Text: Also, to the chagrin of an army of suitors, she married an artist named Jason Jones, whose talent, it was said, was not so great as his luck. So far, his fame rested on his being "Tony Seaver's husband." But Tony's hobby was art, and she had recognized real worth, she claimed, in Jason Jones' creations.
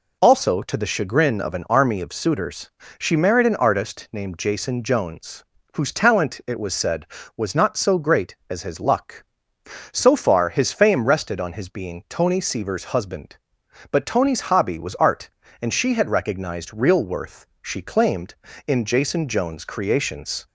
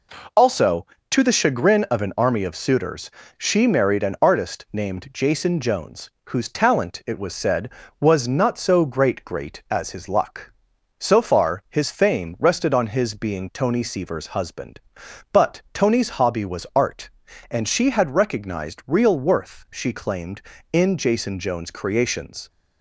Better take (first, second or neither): first